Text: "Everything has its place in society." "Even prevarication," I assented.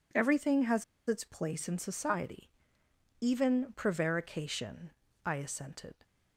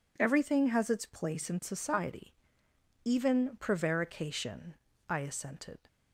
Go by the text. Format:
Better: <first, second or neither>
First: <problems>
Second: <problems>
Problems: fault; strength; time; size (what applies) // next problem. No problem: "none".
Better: second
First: pauses between "has" and "its"; slight; at 0.8 s; 0.23 s long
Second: none